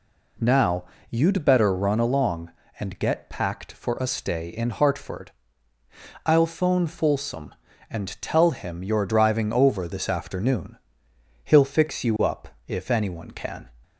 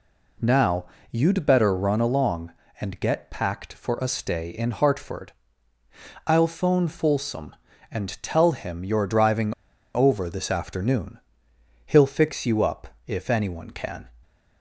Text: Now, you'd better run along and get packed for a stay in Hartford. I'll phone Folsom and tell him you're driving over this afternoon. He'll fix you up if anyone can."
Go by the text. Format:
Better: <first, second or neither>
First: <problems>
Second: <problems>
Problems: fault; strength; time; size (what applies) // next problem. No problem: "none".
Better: first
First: pauses between "up" and "if"; slight; at 12.4 s; 0.18 s long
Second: pauses between "driving" and "over"; at 9.5 s; 0.41 s long // pauses between "up" and "if"; slight; at 12.8 s; 0.18 s long